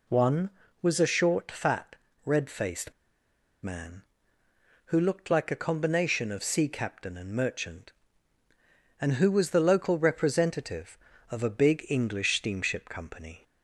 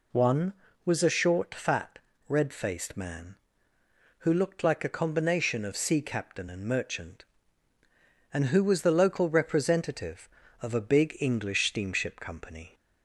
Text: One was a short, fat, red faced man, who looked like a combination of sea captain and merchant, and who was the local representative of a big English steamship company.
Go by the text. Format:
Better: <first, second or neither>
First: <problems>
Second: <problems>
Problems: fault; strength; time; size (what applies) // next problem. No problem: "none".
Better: second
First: pauses between "faced" and "man"; noticeable; at 2.9 s; 0.70 s long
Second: none